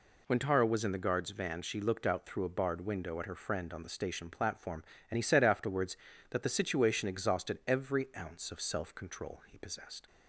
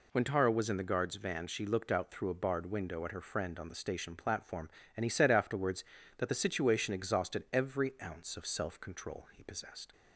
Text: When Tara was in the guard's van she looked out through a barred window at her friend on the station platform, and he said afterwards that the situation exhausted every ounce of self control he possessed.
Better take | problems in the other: neither | none

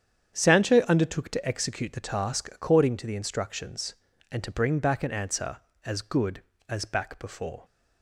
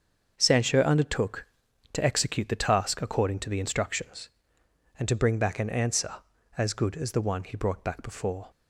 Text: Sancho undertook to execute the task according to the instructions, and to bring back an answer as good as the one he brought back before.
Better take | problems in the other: second | starts louder than the rest; strong; until 1.4 s; 8.5 dB; also in the second // skips "the one he brought"; at 6.8 s

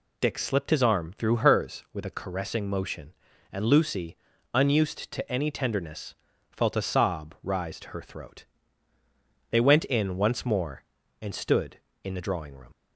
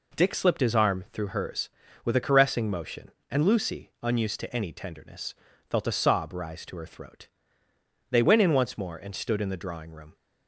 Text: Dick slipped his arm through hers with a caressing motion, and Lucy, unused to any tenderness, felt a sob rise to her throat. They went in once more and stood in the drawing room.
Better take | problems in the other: second | leaves "room" unfinished; at 12.7 s; 45 ms

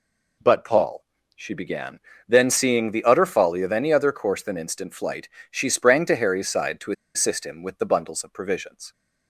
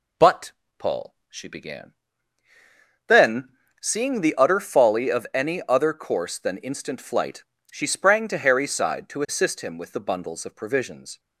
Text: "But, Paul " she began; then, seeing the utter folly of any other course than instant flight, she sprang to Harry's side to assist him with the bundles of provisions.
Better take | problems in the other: second | pauses between "to" and "assist"; slight; at 6.9 s; 0.23 s long

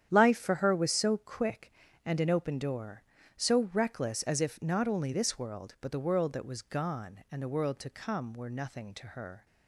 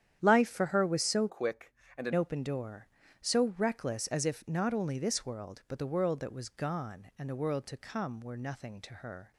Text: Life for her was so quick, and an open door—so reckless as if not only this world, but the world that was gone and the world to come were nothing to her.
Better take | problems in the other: first | starts louder than the rest; strong; until 1.2 s; 10 dB; strong in the first // changes voice from "quick" to "an"; from 1.2 to 2.1 s; 0.9 s long

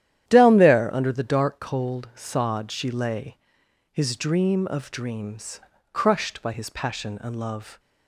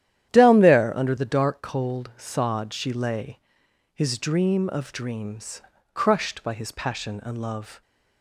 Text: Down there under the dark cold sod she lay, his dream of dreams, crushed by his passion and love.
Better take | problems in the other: neither | starts louder than the rest; strong; the same in both

